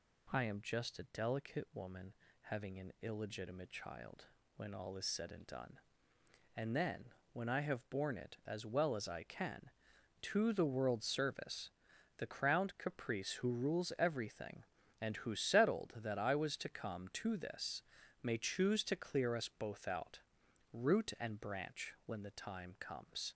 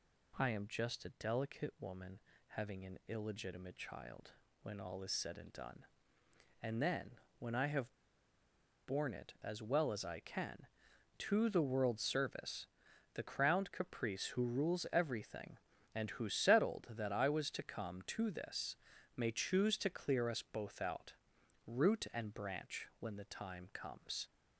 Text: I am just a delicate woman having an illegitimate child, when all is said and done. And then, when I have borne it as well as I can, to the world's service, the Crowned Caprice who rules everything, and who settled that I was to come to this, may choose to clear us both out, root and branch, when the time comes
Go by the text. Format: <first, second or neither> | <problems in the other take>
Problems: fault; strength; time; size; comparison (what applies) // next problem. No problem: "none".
first | pauses between "woman" and "having"; slight; at 2.1 s; 0.30 s long; slight in the first // pauses between "have" and "borne"; noticeable; at 7.9 s; 0.90 s long